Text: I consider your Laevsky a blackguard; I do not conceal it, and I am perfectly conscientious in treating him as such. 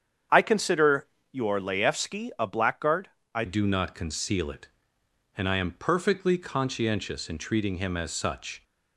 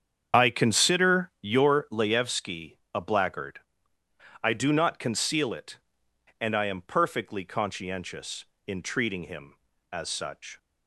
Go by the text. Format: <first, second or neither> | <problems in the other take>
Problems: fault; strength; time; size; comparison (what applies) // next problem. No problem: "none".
second | starts louder than the rest; strong; until 1.5 s; 8 dB; strong in the second // pauses between "consider" and "your"; slight; at 1.0 s; 0.24 s long // changes voice at "do"; from 3.4 s on; 5.2 s long